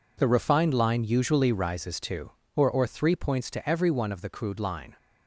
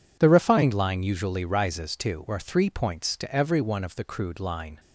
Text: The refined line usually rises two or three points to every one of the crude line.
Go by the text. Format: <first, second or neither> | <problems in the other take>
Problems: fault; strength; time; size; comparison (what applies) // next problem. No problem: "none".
second | says "or" twice; at 2.6 s